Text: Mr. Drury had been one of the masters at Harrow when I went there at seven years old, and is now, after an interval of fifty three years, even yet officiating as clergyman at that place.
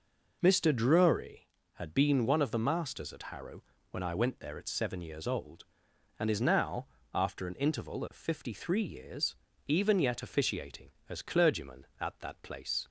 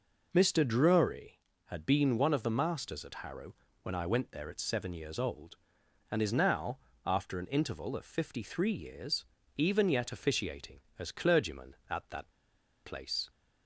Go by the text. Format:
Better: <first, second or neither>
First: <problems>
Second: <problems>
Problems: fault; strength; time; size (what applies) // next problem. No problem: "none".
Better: first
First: pauses between "Harrow" and "when"; slight; at 3.6 s; 0.30 s long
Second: pauses between "Harrow" and "when"; slight; at 3.5 s; 0.30 s long // pauses between "that" and "place"; noticeable; at 12.3 s; 0.52 s long